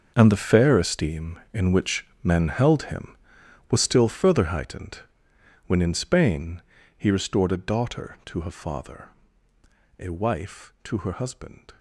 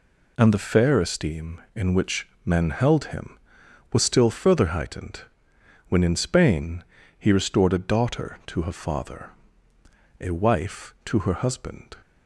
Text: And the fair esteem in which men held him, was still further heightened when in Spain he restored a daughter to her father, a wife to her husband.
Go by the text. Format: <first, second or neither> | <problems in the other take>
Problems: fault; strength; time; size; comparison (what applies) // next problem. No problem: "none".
second | gets quieter; strong; throughout; 14.5 dB // pauses between "which" and "men"; slight; at 2.0 s; 0.18 s long; slight in the second // pauses between "heightened" and "when"; noticeable; at 4.9 s; 0.70 s long; noticeable in the second // pauses between "Spain" and "he"; at 6.6 s; 0.38 s long; also in the second